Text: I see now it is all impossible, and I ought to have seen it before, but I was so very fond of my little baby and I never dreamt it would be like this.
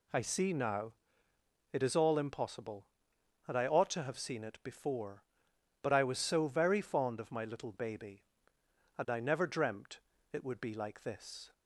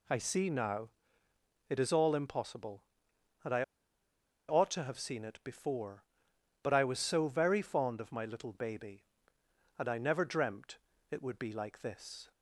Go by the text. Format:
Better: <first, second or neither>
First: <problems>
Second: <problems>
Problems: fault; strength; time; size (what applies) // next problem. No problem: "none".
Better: first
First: pauses between "now" and "it"; noticeable; at 0.9 s; 0.78 s long // pauses between "dreamt" and "it"; slight; at 10.0 s; 0.30 s long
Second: pauses between "now" and "it"; noticeable; at 0.8 s; 0.78 s long // pauses between "I" and "ought"; noticeable; at 3.6 s; 0.85 s long // pauses between "dreamt" and "it"; slight; at 10.7 s; 0.30 s long